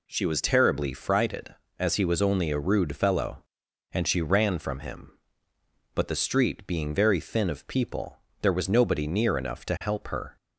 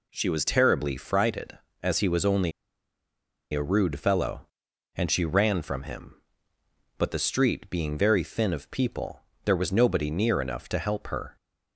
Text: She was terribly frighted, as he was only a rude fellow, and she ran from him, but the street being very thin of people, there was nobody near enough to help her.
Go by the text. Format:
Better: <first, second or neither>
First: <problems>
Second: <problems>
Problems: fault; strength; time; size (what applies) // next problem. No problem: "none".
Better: first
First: none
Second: pauses between "only" and "a"; at 2.5 s; 1.0 s long